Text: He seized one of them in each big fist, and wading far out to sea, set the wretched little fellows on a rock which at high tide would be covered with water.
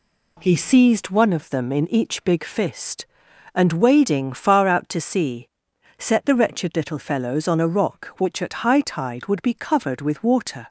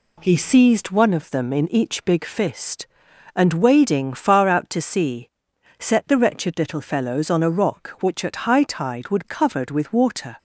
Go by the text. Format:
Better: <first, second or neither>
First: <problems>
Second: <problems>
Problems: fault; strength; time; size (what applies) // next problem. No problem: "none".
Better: first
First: none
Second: skips "be"; at 9.2 s